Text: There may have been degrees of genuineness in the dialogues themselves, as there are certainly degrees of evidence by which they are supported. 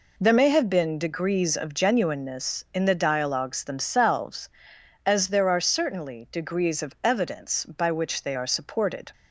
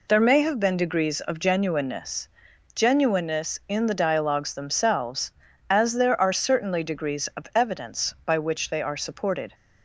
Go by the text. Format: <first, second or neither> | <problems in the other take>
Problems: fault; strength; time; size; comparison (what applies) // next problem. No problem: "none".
first | says "genuineness" twice; at 2.7 s